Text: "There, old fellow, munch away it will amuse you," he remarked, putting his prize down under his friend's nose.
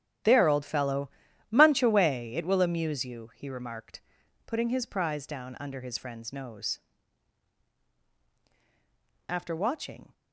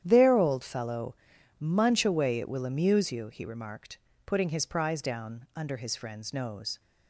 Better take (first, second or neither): second